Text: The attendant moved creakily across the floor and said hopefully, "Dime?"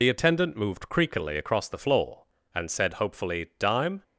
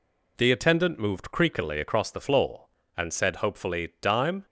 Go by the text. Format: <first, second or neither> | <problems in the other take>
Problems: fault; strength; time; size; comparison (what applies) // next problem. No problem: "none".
second | loses the start of "The"; at 0.0 s; 60 ms